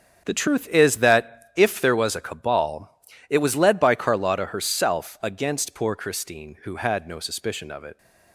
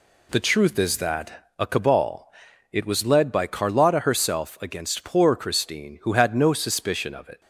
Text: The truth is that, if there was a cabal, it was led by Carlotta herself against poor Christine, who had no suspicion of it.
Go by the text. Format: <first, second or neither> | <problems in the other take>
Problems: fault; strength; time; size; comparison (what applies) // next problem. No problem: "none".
first | skips "if there was"; at 1.5 s